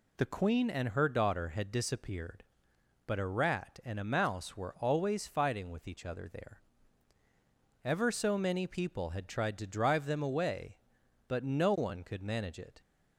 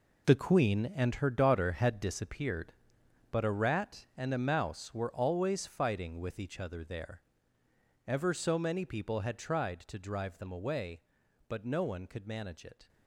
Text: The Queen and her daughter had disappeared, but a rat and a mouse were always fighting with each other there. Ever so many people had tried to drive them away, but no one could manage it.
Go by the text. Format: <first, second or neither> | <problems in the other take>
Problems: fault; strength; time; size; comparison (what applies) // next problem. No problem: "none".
first | gets quieter; strong; throughout; 11 dB